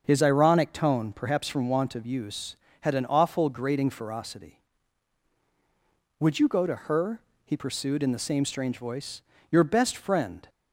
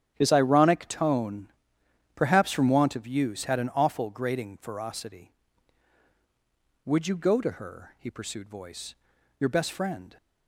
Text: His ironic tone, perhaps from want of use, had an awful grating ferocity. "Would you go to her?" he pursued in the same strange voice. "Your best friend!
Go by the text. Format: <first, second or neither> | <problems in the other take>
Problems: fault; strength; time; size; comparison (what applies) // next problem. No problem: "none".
first | starts louder than the rest; strong; until 1.1 s; 10 dB; also in the first // skips "in the same strange"; at 8.4 s